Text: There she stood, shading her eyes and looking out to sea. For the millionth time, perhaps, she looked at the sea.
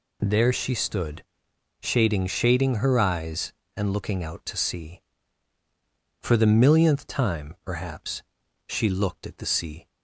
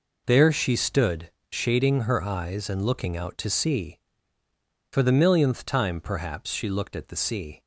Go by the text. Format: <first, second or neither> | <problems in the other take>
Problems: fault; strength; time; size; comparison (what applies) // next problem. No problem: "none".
second | says "shading" twice; at 2.2 s